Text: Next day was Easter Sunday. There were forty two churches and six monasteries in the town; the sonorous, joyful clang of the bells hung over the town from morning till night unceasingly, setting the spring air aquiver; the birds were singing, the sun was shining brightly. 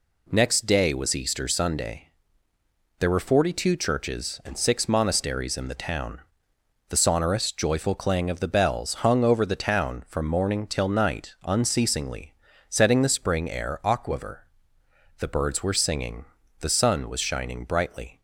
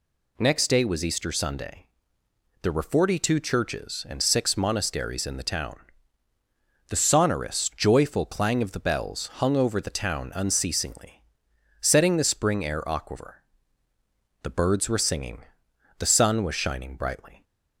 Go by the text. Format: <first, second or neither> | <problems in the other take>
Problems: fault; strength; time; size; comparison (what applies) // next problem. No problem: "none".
first | skips "from morning till night"; at 10.3 s